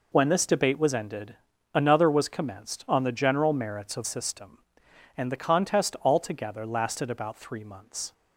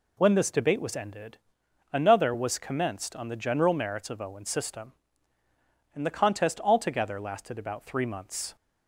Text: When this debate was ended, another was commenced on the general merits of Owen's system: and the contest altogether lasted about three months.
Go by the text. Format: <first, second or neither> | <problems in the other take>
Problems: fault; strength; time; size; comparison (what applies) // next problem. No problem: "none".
second | skips "Owen's"; at 4.0 s